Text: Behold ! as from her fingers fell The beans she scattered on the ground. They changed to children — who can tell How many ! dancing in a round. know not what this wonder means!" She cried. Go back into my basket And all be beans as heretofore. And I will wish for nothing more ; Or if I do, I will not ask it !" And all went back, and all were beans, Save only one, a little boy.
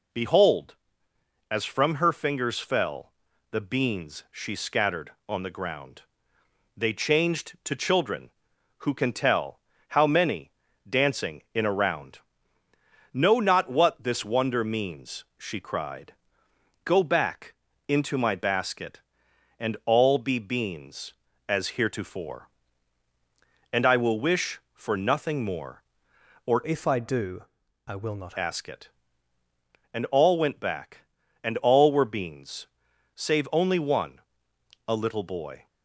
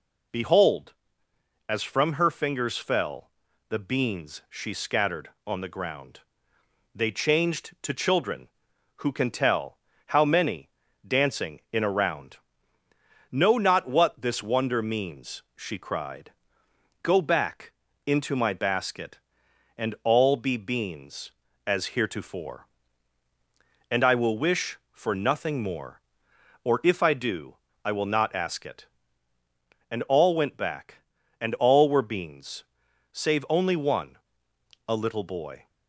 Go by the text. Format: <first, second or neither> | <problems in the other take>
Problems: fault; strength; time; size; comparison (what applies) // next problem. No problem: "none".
second | pauses between "fell" and "The"; at 3.1 s; 0.40 s long; also in the second // pauses between "tell" and "How"; slight; at 9.5 s; 0.30 s long; slight in the second // pauses between "back" and "into"; slight; at 17.5 s; 0.34 s long; slight in the second // changes voice from "if" to "not"; from 26.6 to 28.3 s; 1.7 s long